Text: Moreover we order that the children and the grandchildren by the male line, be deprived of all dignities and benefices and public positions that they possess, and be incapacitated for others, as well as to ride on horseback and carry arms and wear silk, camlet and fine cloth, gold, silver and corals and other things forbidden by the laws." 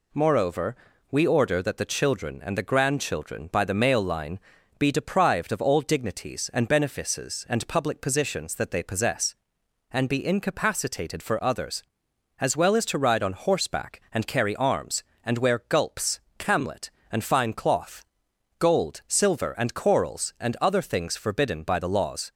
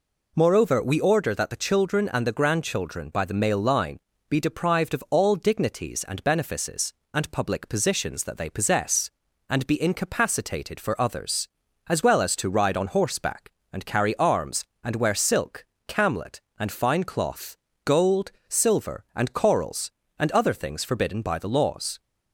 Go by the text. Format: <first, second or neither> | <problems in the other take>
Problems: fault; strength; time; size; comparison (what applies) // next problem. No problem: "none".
second | pauses between "Moreover" and "we"; slight; at 0.7 s; 0.36 s long // says "gulps" for "silk"; at 15.6 s